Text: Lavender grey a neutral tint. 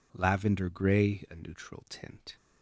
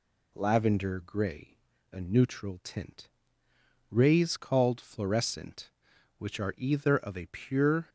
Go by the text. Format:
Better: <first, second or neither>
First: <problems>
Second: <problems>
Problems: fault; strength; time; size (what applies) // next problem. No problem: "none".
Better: first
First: none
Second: pauses between "grey" and "a"; slight; at 1.5 s; 0.34 s long // goes on to say "Rays called fluorescent which are either of a pure"; strong; from 3.9 s on; 3.9 s long